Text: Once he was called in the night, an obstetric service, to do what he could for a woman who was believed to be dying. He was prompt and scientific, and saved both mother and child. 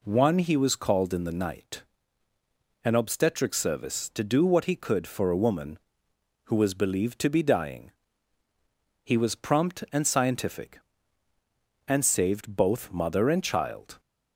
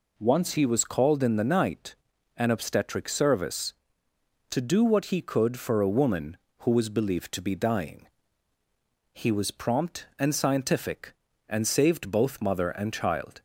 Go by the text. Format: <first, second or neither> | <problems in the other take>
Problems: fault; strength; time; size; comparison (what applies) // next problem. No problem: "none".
second | says "One" for "Once"; at 0.0 s